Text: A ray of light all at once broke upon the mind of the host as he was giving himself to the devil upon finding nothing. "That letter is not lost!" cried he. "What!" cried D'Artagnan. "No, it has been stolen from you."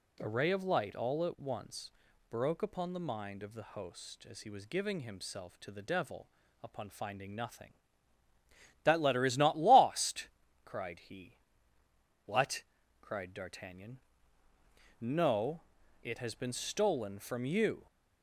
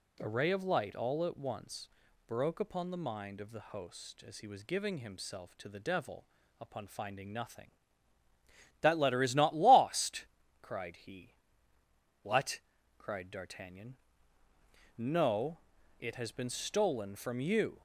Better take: neither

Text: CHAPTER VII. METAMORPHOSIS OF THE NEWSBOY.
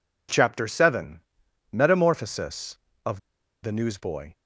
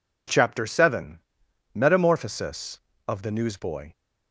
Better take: second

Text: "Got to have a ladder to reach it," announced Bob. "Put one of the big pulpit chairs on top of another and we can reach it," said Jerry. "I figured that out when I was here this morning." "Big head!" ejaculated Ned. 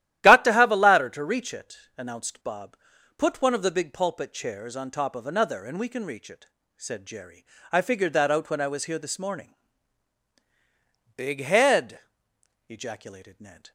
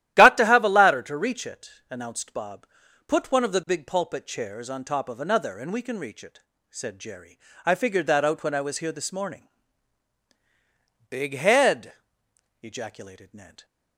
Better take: neither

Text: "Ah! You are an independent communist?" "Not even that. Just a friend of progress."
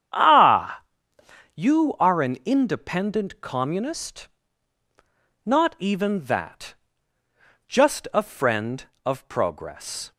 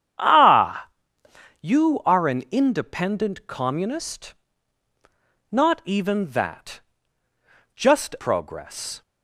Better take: first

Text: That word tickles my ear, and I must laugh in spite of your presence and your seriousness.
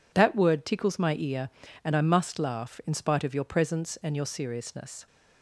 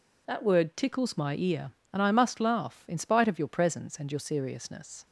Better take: neither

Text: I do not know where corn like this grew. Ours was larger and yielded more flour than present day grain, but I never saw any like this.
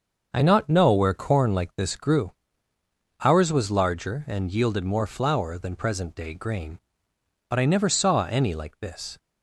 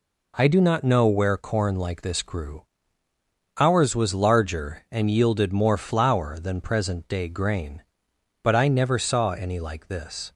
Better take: second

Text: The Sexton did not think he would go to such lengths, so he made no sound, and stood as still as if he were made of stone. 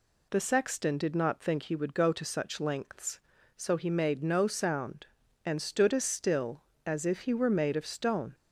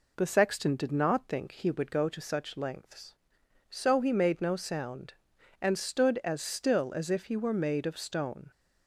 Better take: neither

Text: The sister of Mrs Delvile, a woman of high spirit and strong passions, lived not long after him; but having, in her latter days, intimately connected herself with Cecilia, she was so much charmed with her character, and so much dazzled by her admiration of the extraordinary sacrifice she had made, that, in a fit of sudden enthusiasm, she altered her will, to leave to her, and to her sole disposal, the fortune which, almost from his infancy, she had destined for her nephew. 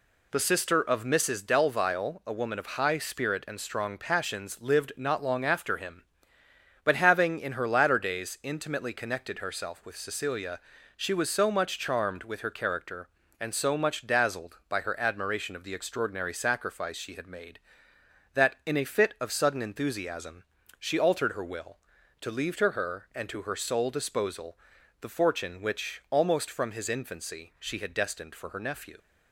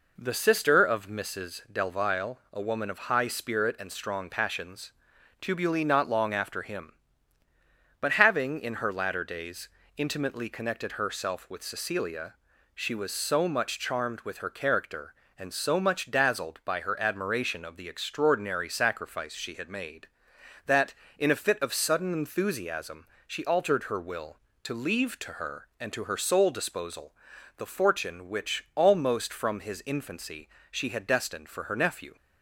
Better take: first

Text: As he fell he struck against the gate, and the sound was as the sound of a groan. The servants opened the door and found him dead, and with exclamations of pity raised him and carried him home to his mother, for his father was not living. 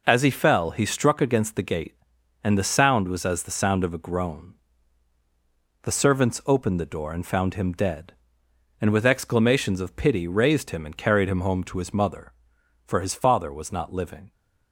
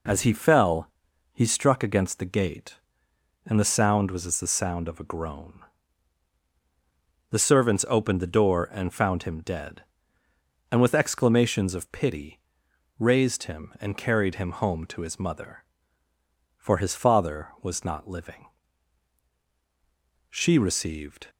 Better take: first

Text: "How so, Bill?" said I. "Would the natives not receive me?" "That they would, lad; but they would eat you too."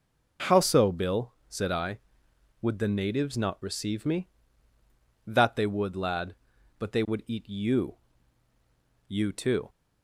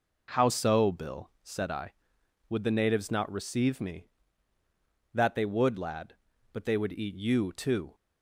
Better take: second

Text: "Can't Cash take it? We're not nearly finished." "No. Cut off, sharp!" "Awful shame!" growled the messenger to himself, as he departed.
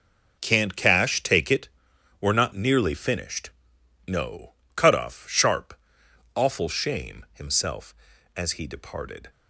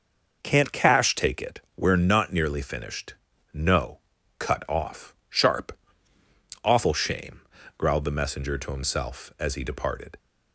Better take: second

